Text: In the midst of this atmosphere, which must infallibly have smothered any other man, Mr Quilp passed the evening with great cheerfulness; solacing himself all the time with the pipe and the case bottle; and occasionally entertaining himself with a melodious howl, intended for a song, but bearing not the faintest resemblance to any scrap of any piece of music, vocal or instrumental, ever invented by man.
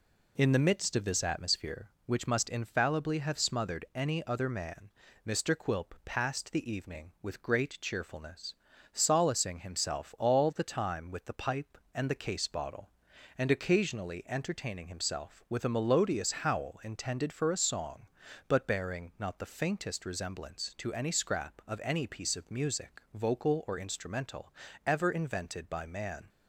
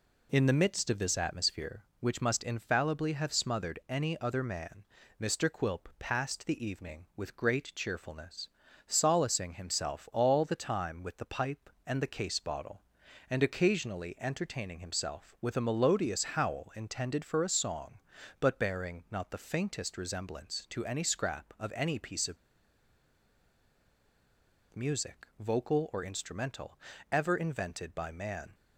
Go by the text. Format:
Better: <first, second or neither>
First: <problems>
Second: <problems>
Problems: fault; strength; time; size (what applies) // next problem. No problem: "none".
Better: first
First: none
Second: pauses between "of" and "music"; strong; at 22.3 s; 2.3 s long